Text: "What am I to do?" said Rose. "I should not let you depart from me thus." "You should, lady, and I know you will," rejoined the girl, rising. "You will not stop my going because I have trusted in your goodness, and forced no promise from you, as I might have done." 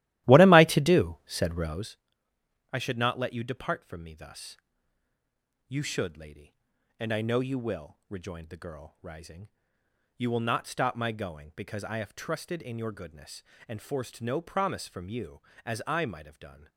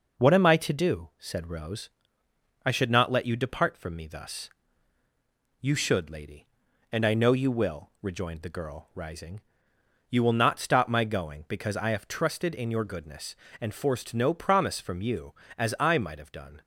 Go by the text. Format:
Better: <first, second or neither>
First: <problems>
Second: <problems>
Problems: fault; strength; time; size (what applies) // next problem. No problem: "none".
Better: second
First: starts louder than the rest; strong; until 1.9 s; 14.5 dB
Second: none